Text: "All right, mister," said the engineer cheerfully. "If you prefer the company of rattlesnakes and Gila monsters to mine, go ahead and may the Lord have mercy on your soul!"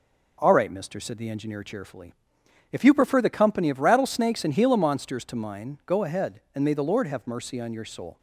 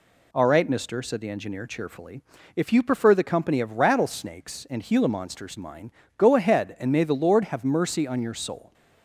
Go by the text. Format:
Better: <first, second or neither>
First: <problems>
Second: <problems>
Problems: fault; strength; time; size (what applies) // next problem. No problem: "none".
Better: first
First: none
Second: skips "to"; at 5.5 s